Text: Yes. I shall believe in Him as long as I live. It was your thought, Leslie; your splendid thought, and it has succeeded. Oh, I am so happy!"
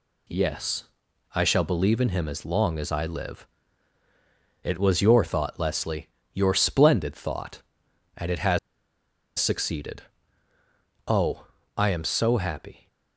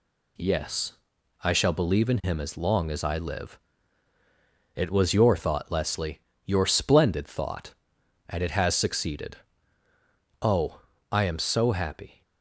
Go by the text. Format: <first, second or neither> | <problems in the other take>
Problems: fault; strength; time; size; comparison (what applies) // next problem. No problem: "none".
second | pauses between "has" and "succeeded"; noticeable; at 8.5 s; 0.80 s long